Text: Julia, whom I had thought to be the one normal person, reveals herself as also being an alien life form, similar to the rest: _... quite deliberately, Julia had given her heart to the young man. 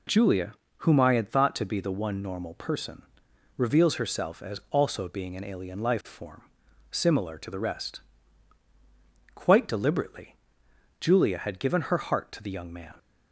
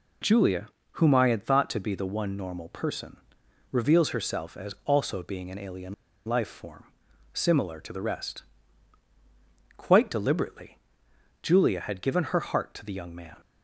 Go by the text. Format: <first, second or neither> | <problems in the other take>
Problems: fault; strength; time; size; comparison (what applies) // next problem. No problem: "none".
first | pauses between "alien" and "life"; slight; at 5.9 s; 0.31 s long